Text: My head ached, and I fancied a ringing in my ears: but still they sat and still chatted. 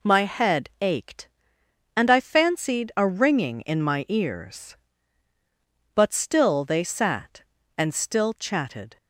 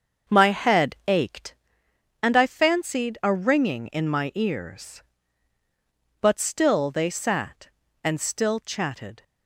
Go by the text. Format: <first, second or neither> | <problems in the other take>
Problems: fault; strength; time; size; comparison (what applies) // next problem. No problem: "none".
first | starts louder than the rest; until 1.8 s; 6.5 dB